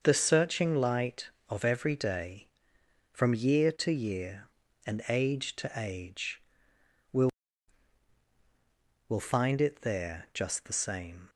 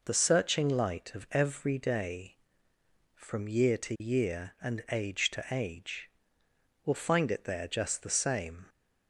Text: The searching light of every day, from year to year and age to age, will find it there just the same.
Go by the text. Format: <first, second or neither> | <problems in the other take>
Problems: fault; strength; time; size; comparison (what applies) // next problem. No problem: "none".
second | starts louder than the rest; until 1.0 s; 6.5 dB // says "will" twice; at 9.0 s